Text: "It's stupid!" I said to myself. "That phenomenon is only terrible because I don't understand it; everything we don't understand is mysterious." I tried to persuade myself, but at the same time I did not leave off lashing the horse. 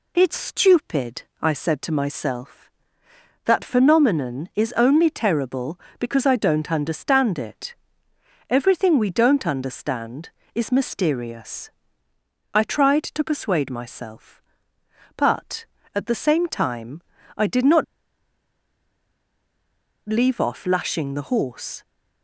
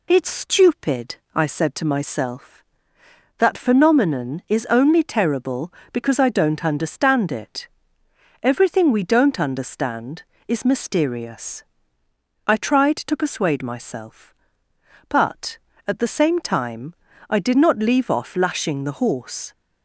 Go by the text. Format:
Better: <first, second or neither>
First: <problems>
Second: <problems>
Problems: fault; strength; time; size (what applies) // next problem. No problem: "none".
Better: second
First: pauses between "time" and "I"; slight; at 17.0 s; 0.34 s long // pauses between "not" and "leave"; strong; at 17.8 s; 2.2 s long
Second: pauses between "time" and "I"; slight; at 16.9 s; 0.34 s long